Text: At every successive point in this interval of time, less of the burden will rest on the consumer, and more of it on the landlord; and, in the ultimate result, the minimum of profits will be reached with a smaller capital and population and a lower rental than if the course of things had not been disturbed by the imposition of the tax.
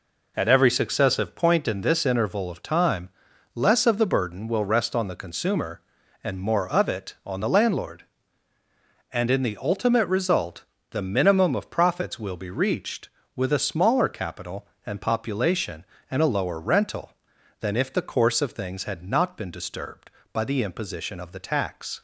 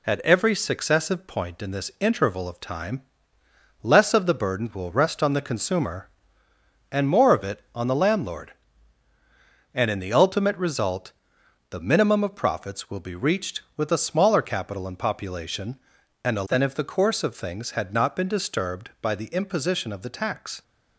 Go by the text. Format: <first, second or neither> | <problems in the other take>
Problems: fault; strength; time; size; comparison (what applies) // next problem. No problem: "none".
first | skips "lower rental"; at 16.4 s